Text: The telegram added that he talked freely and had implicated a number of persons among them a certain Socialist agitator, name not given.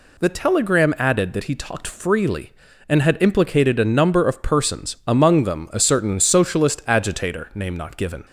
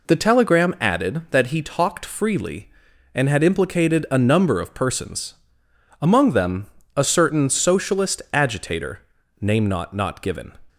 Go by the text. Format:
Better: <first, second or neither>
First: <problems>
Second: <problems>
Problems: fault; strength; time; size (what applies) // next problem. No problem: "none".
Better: first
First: none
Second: pauses between "persons" and "among"; noticeable; at 5.3 s; 0.66 s long // pauses between "them" and "a"; slight; at 6.6 s; 0.32 s long // says "not" twice; at 9.9 s